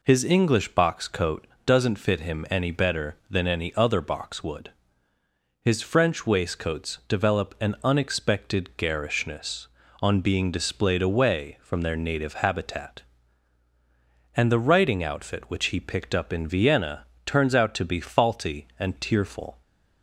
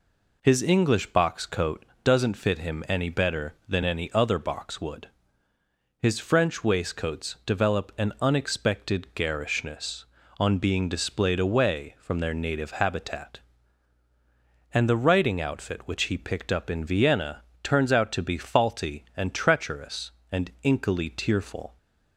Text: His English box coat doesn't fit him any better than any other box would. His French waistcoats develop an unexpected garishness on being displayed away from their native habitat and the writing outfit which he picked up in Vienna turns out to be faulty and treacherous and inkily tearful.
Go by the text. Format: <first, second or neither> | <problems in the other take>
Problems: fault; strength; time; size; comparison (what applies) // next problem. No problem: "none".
second | pauses between "coat" and "doesn't"; slight; at 1.4 s; 0.20 s long; slight in the second // pauses between "Vienna" and "turns"; slight; at 17.0 s; 0.22 s long; slight in the second // skips "treacherous and inkily"; at 18.9 s